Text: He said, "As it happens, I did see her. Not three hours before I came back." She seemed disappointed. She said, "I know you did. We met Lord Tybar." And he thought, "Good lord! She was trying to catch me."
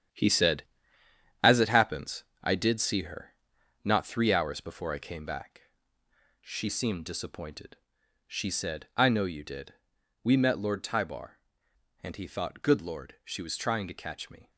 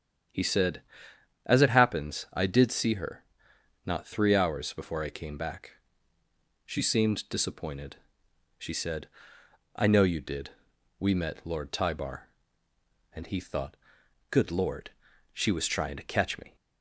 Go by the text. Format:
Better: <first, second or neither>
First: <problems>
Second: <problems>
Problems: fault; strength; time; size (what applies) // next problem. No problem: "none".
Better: second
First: gets quieter; strong; throughout; 8 dB // starts louder than the rest; strong; until 1.9 s; 9.5 dB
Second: starts louder than the rest; strong; until 1.9 s; 8.5 dB